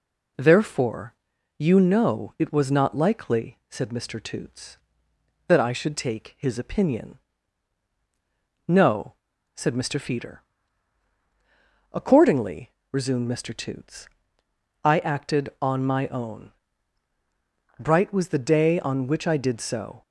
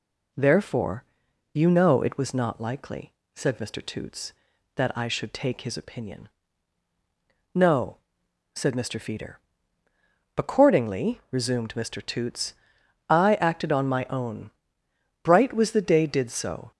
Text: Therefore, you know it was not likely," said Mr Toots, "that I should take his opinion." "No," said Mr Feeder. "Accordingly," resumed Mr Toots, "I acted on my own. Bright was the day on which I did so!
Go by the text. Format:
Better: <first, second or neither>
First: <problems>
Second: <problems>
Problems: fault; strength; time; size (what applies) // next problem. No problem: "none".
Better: first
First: none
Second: skips "on which I"; at 16.0 s